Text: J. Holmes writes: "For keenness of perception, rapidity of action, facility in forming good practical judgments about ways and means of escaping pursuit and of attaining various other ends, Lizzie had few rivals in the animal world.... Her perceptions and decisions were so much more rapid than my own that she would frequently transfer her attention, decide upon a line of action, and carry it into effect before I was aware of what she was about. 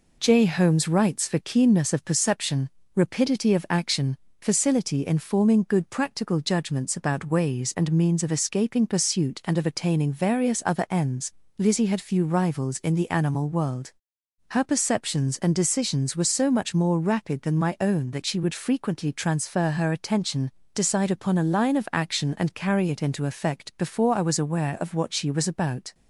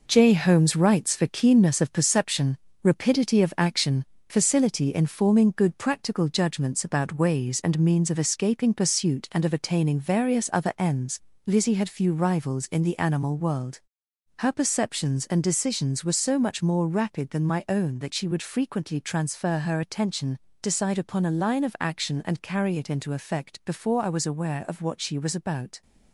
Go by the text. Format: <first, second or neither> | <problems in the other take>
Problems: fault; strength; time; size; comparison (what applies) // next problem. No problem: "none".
first | gets quieter; throughout; 6.5 dB